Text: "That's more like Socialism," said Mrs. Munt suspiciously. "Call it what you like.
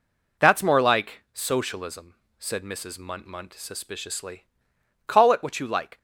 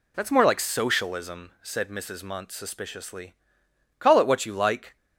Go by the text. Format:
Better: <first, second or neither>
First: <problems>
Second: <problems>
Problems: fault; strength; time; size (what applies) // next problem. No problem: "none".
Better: second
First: says "Munt" twice; at 3.2 s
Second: none